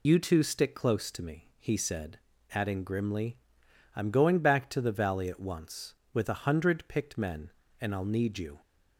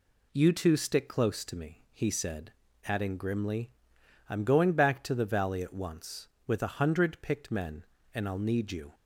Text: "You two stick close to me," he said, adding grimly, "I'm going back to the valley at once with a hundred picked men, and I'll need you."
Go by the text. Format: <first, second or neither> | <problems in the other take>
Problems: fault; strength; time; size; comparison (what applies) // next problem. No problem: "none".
second | loses the start of "You"; at 0.0 s; 75 ms